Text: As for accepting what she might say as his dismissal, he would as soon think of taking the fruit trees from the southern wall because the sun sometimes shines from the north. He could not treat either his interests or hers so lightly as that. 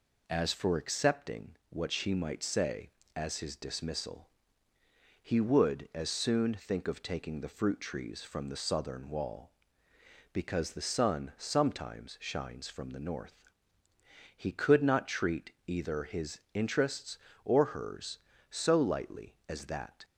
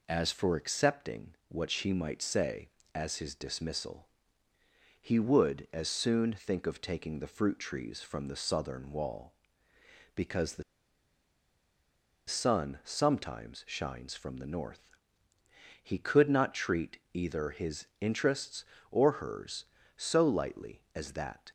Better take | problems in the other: first | pauses between "the" and "sun"; strong; at 10.6 s; 1.6 s long // pauses between "treat" and "either"; slight; at 16.9 s; 0.16 s long; slight in the first // pauses between "his" and "interests"; slight; at 17.8 s; 0.16 s long; slight in the first

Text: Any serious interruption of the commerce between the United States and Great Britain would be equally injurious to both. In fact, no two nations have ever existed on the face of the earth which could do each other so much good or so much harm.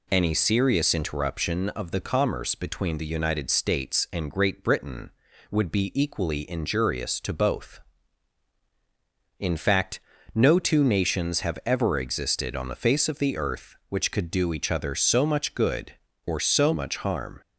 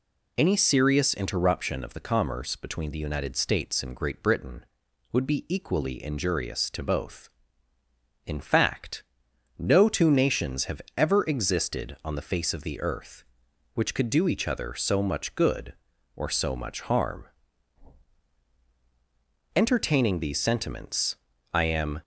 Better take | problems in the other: first | pauses between "have" and "ever"; slight; at 10.7 s; 0.16 s long // goes on to say "Entertaining these sentiments I am"; strong; from 19.5 s on; 2.4 s long

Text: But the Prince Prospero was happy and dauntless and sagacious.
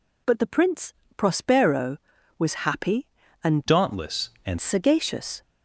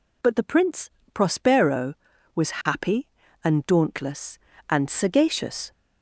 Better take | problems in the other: second | pauses between "Prince" and "Prospero"; slight; at 0.9 s; 0.22 s long; slight in the second // changes voice from "dauntless" to "and"; from 3.6 to 4.5 s; 0.9 s long

